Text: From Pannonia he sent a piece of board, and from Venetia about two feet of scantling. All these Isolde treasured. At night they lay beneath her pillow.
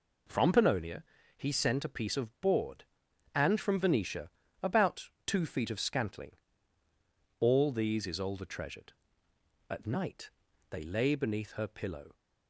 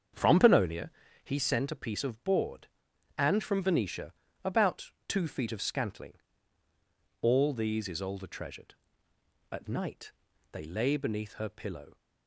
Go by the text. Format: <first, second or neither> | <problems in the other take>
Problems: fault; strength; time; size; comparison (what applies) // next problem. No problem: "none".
first | starts louder than the rest; strong; until 1.4 s; 7.5 dB // pauses between "Pannonia" and "he"; slight; at 0.9 s; 0.34 s long; slight in the first // pauses between "Venetia" and "about"; slight; at 4.1 s; 0.32 s long; slight in the first // pauses between "about" and "two"; slight; at 4.9 s; 0.16 s long; slight in the first // pauses between "night" and "they"; at 10.1 s; 0.40 s long; also in the first